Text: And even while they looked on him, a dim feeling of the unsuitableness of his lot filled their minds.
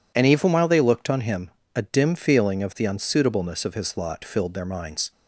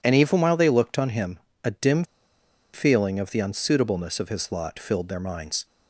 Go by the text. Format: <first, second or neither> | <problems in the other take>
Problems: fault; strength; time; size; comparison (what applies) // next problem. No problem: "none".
first | pauses between "dim" and "feeling"; noticeable; at 2.0 s; 0.70 s long